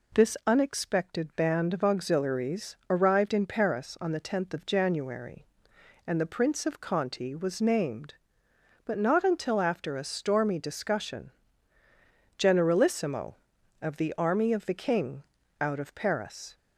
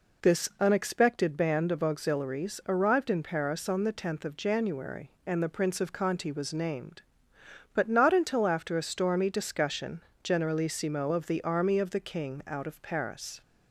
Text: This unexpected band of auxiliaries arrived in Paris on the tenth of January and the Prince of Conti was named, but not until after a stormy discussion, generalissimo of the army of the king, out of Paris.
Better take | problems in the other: neither | none

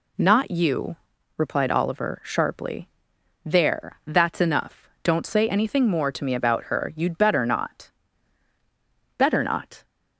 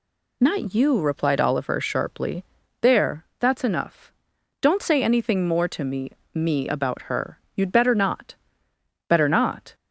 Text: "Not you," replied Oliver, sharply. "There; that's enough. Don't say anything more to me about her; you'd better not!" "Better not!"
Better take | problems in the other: first | says "me" twice; at 6.3 s

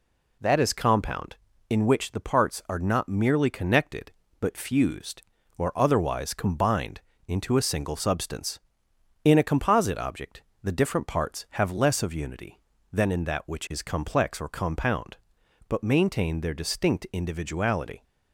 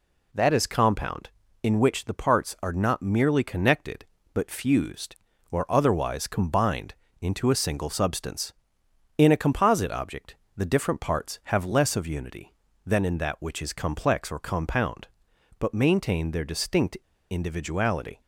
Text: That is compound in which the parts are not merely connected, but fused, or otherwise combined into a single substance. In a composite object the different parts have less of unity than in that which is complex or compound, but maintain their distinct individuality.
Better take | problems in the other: first | pauses between "combined" and "into"; slight; at 6.9 s; 0.26 s long; slight in the first // pauses between "object" and "the"; slight; at 10.3 s; 0.20 s long; slight in the first // pauses between "distinct" and "individuality"; slight; at 16.9 s; 0.33 s long

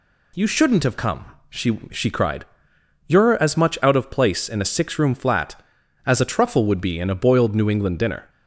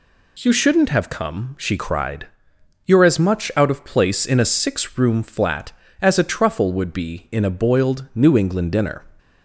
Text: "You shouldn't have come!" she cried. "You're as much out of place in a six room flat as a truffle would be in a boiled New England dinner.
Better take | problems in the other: second | says "she" twice; at 1.9 s

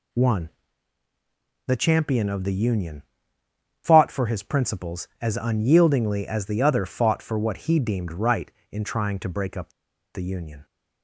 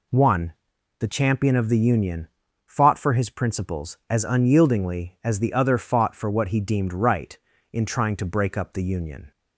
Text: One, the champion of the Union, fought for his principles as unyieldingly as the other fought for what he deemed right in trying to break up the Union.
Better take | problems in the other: second | pauses between "up" and "the"; at 9.7 s; 0.42 s long

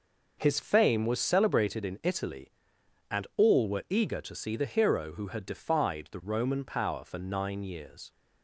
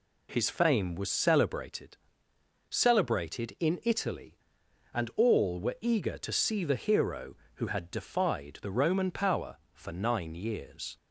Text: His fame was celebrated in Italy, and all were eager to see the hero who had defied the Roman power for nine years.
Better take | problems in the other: first | says "celebrated" twice; at 2.7 s

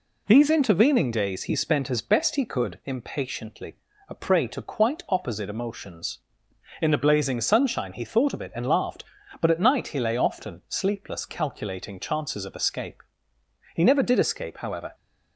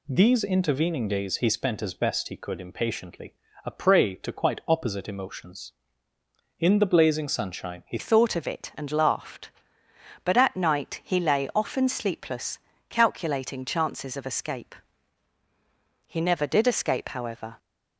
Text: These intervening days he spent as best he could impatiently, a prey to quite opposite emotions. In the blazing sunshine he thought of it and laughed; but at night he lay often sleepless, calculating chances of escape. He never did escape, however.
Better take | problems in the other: first | changes voice at "thought"; from 7.9 s on; 9.6 s long

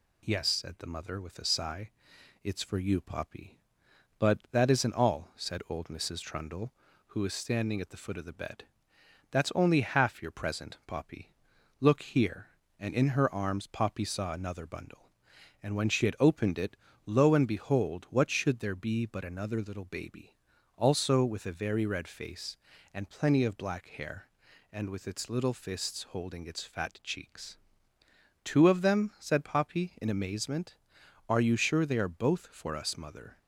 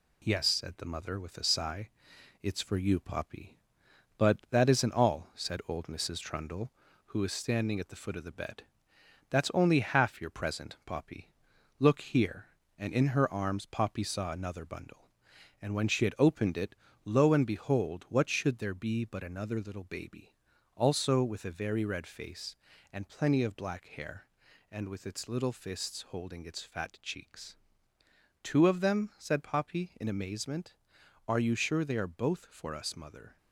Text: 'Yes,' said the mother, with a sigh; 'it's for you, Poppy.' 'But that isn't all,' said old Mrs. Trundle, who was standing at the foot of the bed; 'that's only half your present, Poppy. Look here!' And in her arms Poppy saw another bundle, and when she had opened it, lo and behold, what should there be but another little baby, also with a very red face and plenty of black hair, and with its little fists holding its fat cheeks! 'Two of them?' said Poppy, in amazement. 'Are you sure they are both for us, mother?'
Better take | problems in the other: first | gets quieter; slight; throughout; 3.5 dB

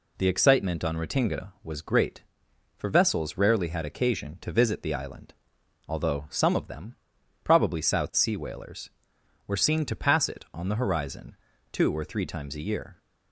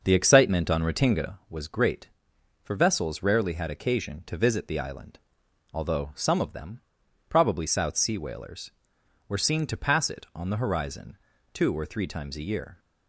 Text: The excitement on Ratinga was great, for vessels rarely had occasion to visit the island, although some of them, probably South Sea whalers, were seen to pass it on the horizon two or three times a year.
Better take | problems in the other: first | starts louder than the rest; until 1.4 s; 6 dB // pauses between "horizon" and "two"; slight; at 11.1 s; 0.36 s long; slight in the first

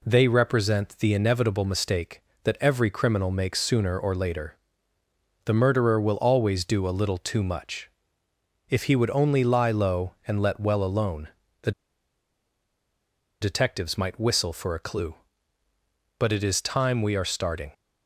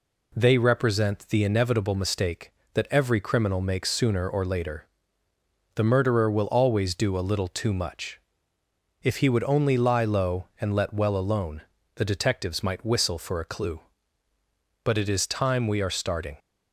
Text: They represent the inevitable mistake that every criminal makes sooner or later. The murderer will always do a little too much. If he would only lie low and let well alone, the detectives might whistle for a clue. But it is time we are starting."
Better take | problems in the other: second | pauses between "the" and "detectives"; strong; at 11.7 s; 1.7 s long

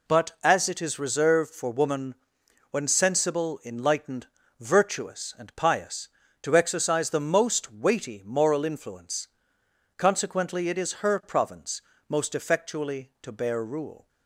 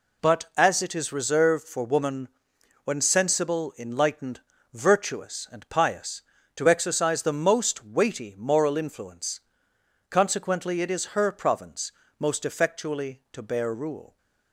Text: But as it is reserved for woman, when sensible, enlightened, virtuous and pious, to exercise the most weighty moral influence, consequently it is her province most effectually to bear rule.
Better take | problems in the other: neither | pauses between "province" and "most"; slight; the same in both

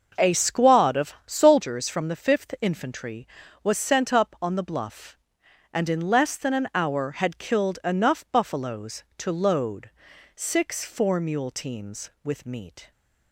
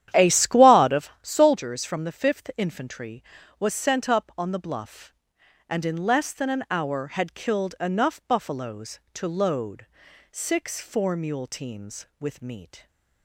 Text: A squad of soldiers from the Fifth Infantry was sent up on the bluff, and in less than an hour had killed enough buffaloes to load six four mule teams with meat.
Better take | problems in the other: first | starts louder than the rest; strong; until 1.1 s; 10.5 dB // pauses between "load" and "six"; noticeable; at 9.8 s; 0.46 s long; noticeable in the first

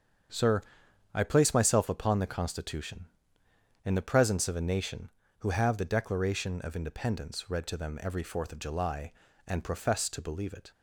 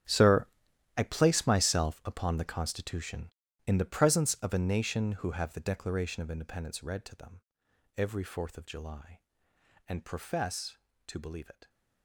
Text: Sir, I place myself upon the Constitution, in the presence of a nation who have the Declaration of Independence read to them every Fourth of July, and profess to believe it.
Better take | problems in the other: first | gets quieter; strong; throughout; 17 dB // starts louder than the rest; strong; until 1.6 s; 9.5 dB; strong in the first // pauses between "them" and "every"; noticeable; at 7.4 s; 0.56 s long

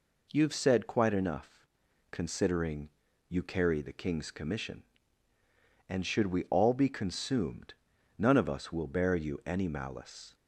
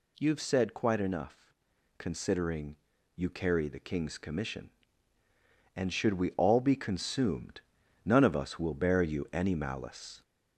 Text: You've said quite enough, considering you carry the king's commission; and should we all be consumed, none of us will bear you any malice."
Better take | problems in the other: first | gets louder; throughout; 4 dB // pauses between "considering" and "you"; at 2.7 s; 0.38 s long; also in the first

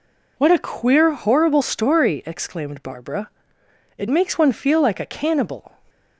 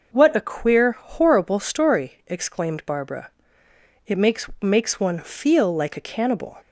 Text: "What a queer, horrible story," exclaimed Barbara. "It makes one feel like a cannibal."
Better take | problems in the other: first | says "makes" twice; at 4.5 s

